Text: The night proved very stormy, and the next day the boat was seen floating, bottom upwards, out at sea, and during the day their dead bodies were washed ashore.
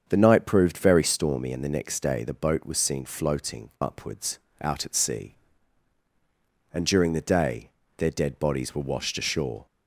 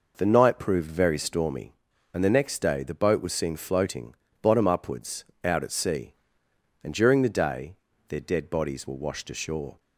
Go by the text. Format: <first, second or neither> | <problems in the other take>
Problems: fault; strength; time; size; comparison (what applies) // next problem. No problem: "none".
second | starts louder than the rest; strong; until 1.0 s; 7 dB // skips "bottom"; at 3.7 s // pauses between "day" and "their"; slight; at 7.6 s; 0.26 s long; slight in the second